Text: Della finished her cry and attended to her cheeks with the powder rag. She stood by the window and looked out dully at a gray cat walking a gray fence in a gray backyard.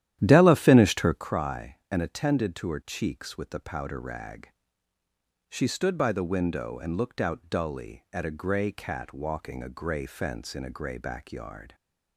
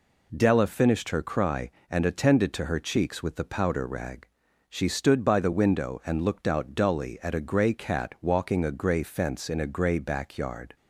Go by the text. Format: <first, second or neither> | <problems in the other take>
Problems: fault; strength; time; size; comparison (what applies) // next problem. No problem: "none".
second | starts louder than the rest; strong; until 1.2 s; 11.5 dB